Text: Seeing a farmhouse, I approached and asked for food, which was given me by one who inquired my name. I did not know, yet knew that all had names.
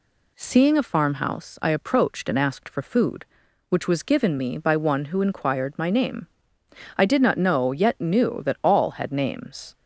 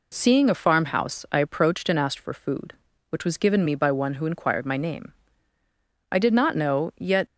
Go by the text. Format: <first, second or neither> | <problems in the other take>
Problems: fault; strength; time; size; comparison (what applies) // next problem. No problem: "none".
first | stops before "knew that all had names"; at 7.2 s